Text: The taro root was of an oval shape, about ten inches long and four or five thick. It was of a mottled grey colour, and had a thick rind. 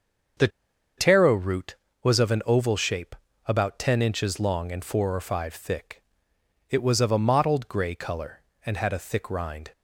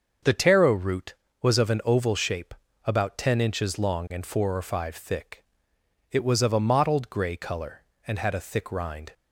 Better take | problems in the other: second | starts louder than the rest; until 2.1 s; 6.5 dB; also in the second // pauses between "The" and "taro"; noticeable; at 0.4 s; 0.49 s long

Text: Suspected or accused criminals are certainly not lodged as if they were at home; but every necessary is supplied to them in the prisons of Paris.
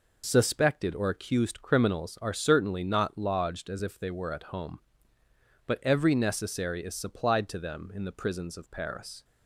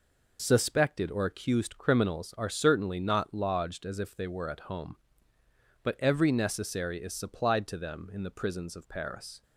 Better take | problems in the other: neither | none

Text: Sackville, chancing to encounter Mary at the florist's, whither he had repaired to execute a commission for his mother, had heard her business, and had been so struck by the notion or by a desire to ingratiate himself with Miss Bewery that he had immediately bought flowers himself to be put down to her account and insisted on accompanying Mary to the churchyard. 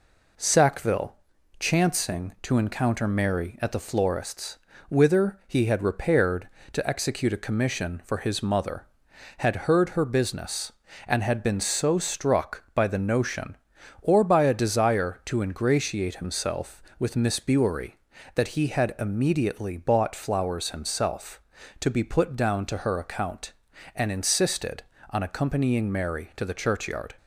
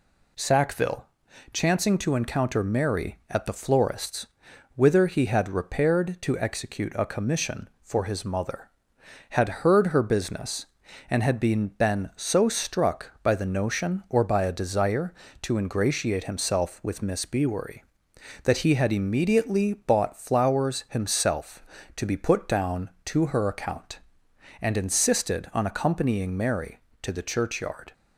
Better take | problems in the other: first | says "been" twice; at 11.6 s

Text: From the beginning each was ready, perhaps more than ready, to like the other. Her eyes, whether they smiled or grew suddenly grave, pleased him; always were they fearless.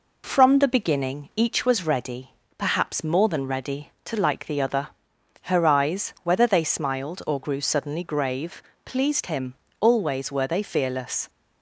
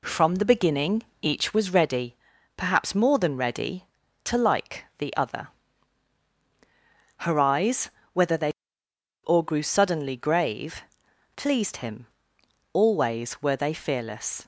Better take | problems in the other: first | pauses between "beginning" and "each"; slight; at 1.0 s; 0.20 s long // skips "smiled"; at 8.8 s

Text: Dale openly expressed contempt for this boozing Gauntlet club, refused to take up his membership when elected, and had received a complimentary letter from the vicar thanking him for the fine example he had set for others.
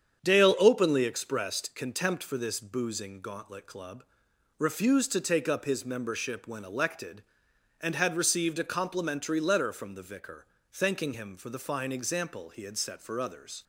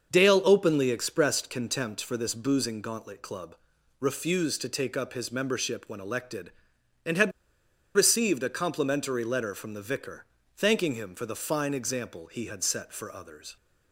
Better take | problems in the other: first | starts louder than the rest; until 1.1 s; 6.5 dB; strong in the first // pauses between "had" and "received"; noticeable; at 7.3 s; 0.64 s long // pauses between "vicar" and "thanking"; slight; at 10.2 s; 0.32 s long; slight in the first

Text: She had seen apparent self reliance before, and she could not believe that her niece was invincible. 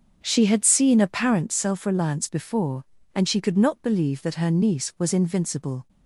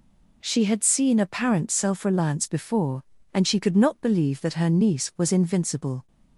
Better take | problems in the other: second | starts louder than the rest; until 1.4 s; 6.5 dB

